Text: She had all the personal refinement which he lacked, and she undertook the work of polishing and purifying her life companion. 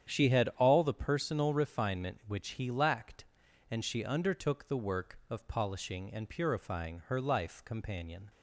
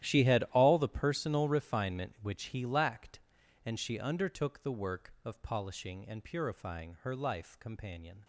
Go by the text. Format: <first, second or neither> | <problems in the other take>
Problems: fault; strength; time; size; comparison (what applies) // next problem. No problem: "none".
first | gets quieter; strong; throughout; 16.5 dB // starts louder than the rest; strong; until 1.1 s; 12.5 dB; strong in the first